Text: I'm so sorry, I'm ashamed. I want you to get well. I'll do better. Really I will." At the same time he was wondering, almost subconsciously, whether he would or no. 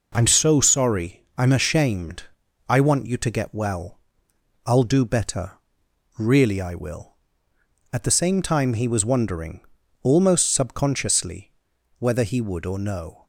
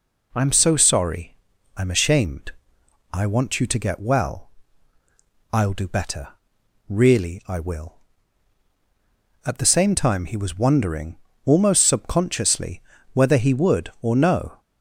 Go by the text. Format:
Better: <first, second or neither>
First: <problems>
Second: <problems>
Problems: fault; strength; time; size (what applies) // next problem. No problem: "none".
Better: neither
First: none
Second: none